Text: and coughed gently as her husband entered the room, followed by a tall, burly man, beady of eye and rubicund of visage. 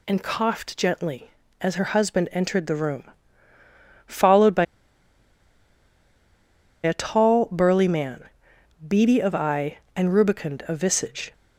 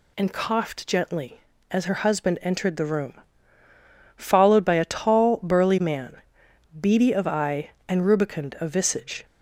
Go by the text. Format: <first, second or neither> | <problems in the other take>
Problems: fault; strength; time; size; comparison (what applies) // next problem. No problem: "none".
second | pauses between "by" and "a"; strong; at 4.6 s; 2.1 s long